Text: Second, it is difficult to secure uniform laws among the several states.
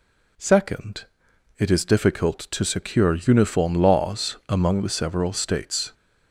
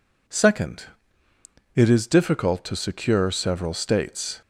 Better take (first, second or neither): first